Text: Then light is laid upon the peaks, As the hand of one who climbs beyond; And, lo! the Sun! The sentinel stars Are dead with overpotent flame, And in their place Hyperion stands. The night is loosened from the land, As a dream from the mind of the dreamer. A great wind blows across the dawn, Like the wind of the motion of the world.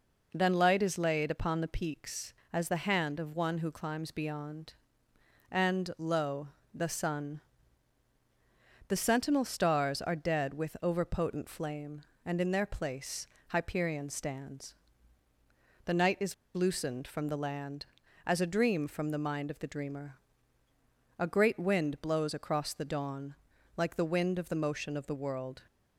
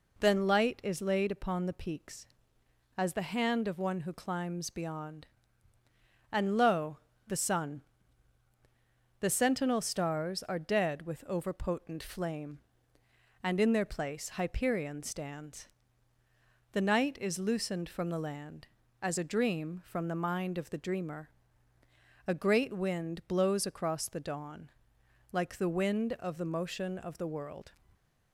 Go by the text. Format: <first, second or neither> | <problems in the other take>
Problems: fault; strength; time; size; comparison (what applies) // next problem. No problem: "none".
second | pauses between "place" and "Hyperion"; slight; at 13.2 s; 0.22 s long // pauses between "is" and "loosened"; slight; at 16.3 s; 0.20 s long